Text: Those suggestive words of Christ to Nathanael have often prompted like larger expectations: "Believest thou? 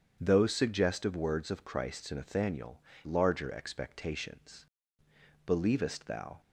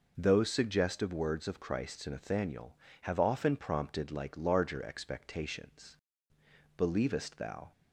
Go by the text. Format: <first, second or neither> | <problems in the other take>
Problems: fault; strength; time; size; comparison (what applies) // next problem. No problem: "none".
second | starts louder than the rest; strong; until 1.2 s; 7.5 dB // skips "have often prompted like"; at 2.9 s